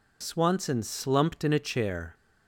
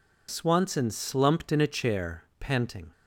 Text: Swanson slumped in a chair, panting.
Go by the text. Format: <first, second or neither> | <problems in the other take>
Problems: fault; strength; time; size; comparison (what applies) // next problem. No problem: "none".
second | stops before "panting"; at 2.1 s